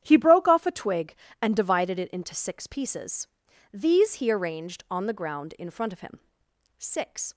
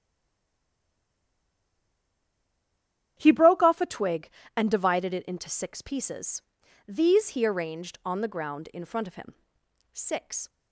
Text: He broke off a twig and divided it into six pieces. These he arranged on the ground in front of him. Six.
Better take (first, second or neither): first